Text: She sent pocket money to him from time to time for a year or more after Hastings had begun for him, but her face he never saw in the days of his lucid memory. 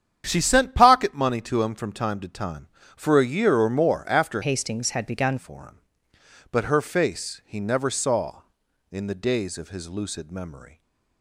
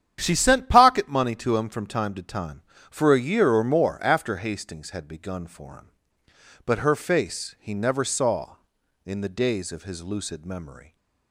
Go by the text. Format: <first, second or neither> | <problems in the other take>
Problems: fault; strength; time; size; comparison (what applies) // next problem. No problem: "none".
second | starts louder than the rest; strong; until 1.2 s; 9 dB; strong in the second // changes voice from "Hastings" to "begun"; from 4.4 to 5.3 s; 0.9 s long // stays silent after the last word; slight; from 10.6 s on; 0.6 s long